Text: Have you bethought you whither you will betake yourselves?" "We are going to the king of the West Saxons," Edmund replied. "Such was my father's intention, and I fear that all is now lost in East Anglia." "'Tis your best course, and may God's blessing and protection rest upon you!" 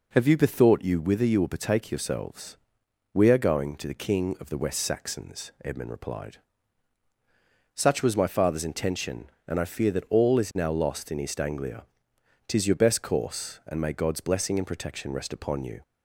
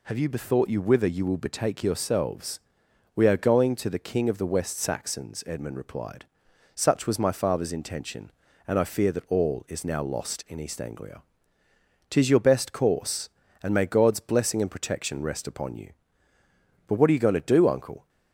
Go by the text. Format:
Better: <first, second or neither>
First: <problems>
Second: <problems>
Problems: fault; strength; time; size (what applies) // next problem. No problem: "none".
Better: first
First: none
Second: goes on to say "But what are you going to do uncle"; noticeable; from 16.8 s on; 1.2 s long